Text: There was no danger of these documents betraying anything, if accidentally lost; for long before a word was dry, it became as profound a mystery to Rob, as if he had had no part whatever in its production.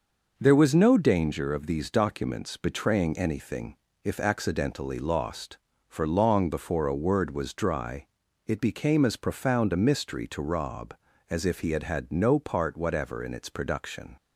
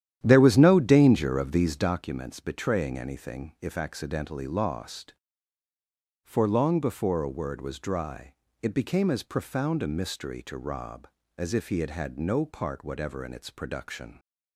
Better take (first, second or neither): first